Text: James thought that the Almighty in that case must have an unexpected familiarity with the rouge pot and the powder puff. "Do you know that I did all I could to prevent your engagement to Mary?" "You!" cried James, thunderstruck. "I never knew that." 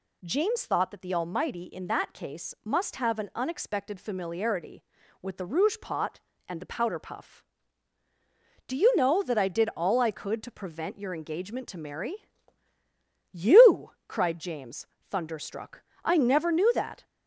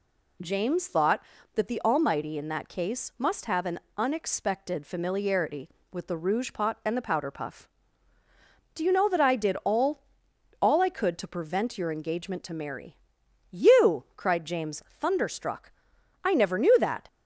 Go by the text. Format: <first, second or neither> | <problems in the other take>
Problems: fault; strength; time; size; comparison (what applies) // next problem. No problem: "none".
first | pauses between "an" and "unexpected"; slight; at 3.7 s; 0.18 s long // says "all" twice; at 10.6 s